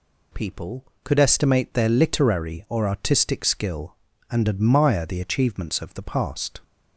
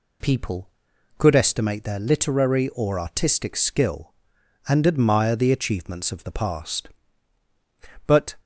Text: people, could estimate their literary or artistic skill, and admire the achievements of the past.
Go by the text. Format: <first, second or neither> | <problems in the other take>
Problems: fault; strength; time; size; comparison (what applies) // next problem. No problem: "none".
first | goes on to say "But"; slight; from 8.0 s on; 0.28 s long